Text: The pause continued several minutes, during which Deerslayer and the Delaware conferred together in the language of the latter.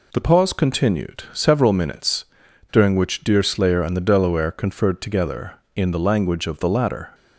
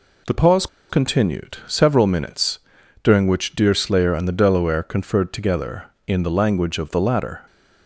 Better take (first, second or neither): first